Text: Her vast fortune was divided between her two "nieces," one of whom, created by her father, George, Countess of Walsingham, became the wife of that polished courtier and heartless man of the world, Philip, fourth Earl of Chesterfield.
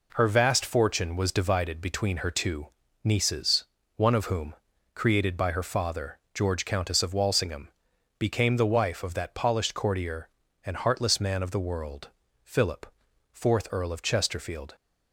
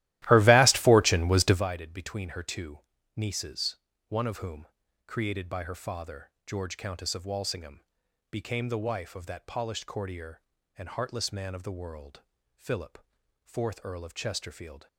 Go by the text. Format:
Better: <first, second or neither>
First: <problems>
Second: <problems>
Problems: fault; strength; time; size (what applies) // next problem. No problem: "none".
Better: first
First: pauses between "two" and "nieces"; slight; at 2.6 s; 0.34 s long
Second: starts louder than the rest; strong; until 1.6 s; 15.5 dB // pauses between "two" and "nieces"; slight; at 2.7 s; 0.34 s long